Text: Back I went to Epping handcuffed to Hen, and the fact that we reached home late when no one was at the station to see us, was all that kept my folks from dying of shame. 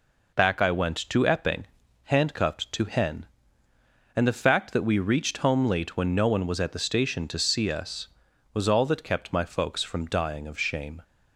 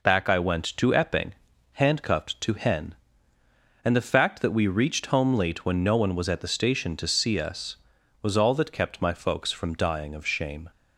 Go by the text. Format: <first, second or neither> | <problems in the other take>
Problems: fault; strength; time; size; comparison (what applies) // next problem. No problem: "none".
neither | pauses between "Epping" and "handcuffed"; the same in both